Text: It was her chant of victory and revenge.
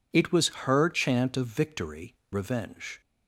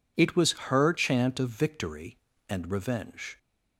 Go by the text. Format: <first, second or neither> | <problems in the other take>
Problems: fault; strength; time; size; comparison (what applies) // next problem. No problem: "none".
second | skips "and"; at 2.2 s